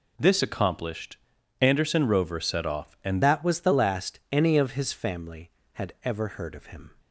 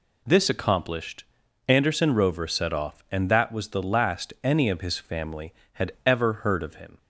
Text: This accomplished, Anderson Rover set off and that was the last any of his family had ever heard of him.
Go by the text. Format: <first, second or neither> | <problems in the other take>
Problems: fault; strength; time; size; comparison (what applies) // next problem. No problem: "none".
second | changes voice at "that"; from 3.2 s on; 3.6 s long